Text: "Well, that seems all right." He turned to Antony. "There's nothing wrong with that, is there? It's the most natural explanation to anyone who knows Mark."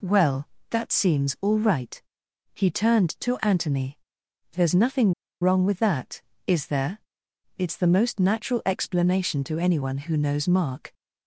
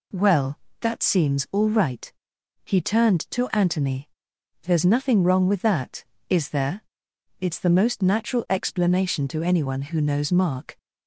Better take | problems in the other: second | pauses between "nothing" and "wrong"; slight; at 5.1 s; 0.28 s long

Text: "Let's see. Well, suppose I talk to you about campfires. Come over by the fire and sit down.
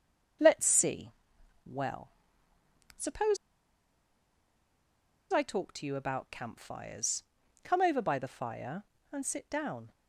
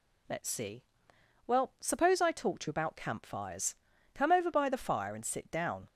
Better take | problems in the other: second | starts louder than the rest; until 1.9 s; 6.5 dB // pauses between "suppose" and "I"; strong; at 3.3 s; 1.9 s long

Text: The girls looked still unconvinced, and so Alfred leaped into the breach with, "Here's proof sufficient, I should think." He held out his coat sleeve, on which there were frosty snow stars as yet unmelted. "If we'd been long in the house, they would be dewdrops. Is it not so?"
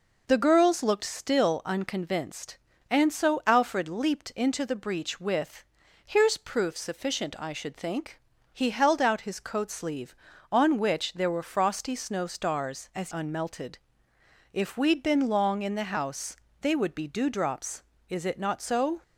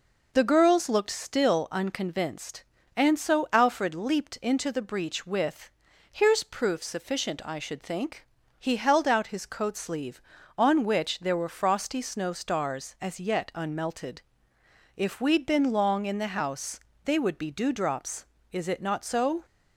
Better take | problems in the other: second | skips "yet"; at 13.1 s

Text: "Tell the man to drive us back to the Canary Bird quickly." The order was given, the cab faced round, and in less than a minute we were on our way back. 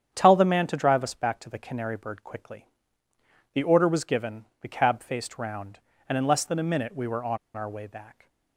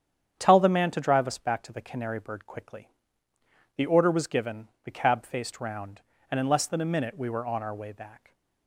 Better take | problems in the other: second | starts louder than the rest; strong; until 1.1 s; 8.5 dB; strong in the second // pauses between "on" and "our"; slight; at 7.3 s; 0.18 s long

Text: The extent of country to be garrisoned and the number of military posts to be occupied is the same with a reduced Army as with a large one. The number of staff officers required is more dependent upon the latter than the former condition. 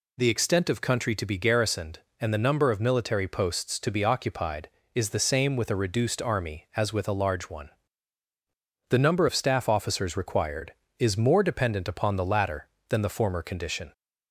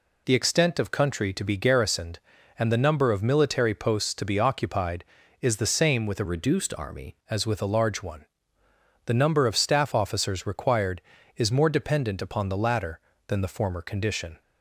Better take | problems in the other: first | changes voice from "reduced" to "Army"; from 6.2 to 7.1 s; 0.9 s long

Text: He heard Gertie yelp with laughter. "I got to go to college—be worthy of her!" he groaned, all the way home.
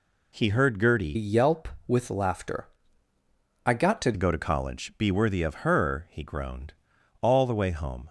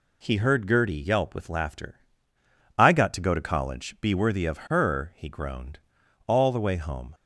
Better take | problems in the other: second | changes voice from "yelp" to "to"; from 1.1 to 4.1 s; 3.0 s long

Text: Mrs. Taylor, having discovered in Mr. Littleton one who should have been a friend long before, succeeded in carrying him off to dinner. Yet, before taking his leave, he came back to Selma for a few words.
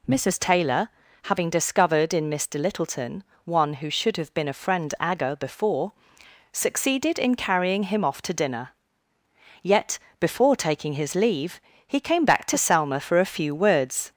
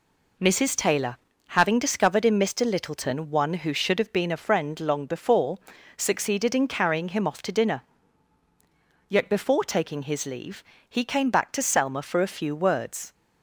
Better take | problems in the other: second | pauses between "Littleton" and "one"; slight; at 3.2 s; 0.22 s long // says "agger" for "long"; at 4.9 s

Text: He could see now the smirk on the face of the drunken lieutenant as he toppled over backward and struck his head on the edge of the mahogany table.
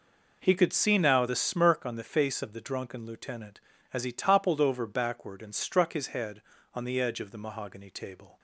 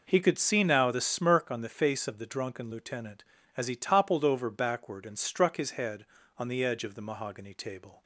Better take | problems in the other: neither | none

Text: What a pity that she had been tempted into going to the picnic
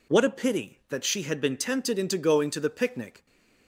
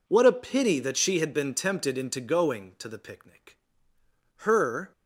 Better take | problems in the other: first | goes on to say "Her"; from 4.3 s on; 0.56 s long

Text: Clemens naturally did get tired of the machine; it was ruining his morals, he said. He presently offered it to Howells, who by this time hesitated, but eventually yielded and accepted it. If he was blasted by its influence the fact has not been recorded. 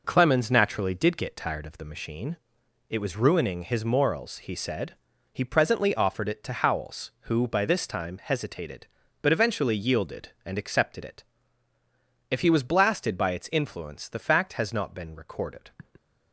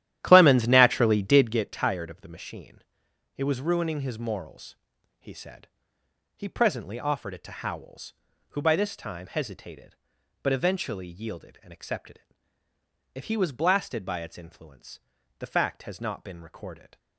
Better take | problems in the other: first | starts louder than the rest; strong; until 1.7 s; 12 dB // pauses between "influence" and "the"; at 14.9 s; 0.40 s long

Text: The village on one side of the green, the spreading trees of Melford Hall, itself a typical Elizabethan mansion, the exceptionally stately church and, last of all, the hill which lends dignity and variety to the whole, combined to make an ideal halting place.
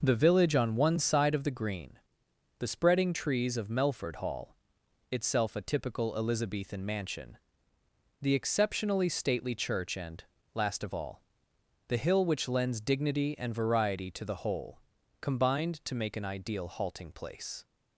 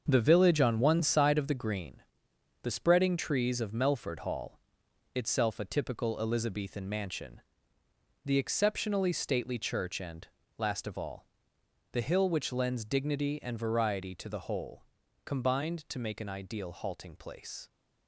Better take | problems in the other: first | gets quieter; strong; throughout; 8.5 dB

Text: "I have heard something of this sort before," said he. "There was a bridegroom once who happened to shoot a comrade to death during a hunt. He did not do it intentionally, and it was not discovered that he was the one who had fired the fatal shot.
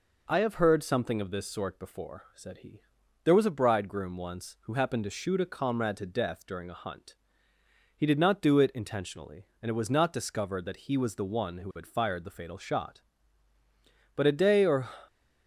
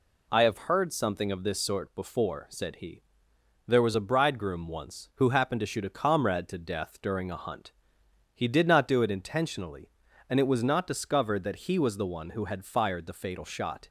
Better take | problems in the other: second | goes on to say "But a day or"; noticeable; from 14.1 s on; 0.76 s long

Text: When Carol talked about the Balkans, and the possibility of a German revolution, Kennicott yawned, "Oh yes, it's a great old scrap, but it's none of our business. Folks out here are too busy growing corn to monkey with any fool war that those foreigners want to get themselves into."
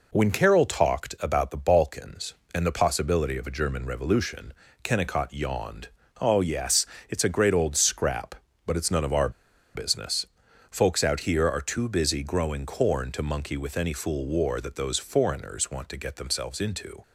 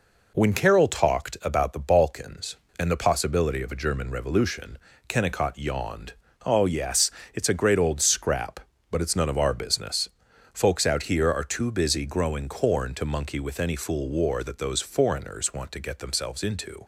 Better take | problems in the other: second | pauses between "our" and "business"; at 9.2 s; 0.44 s long

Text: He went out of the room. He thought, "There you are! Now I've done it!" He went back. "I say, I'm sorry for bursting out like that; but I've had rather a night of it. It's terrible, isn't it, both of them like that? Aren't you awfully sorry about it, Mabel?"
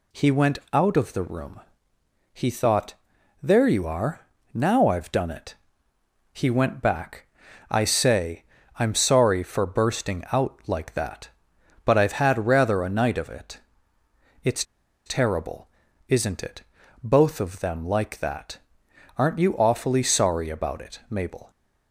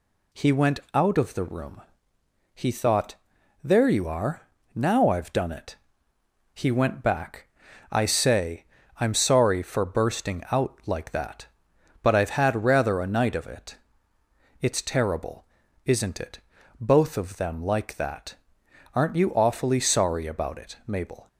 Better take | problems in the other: second | pauses between "went" and "out"; slight; at 0.5 s; 0.16 s long; slight in the second // pauses between "It's" and "terrible"; at 14.6 s; 0.42 s long

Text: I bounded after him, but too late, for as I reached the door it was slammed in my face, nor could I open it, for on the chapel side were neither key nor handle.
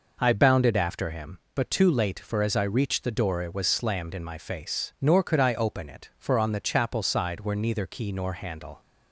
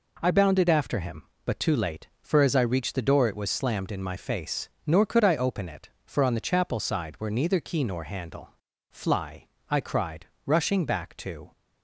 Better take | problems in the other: first | goes on to say "Fly I cried rushing back to"; strong; from 8.8 s on; 2.6 s long

